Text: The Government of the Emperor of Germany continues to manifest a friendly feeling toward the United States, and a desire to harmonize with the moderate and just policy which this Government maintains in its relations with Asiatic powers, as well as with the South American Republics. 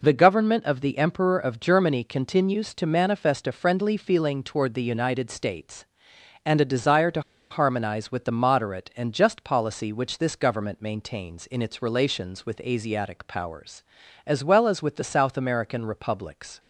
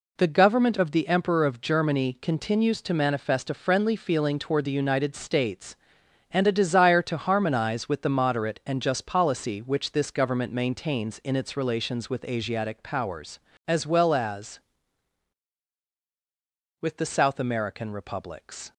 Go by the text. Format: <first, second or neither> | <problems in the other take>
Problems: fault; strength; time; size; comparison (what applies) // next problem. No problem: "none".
second | pauses between "to" and "harmonize"; slight; at 7.1 s; 0.30 s long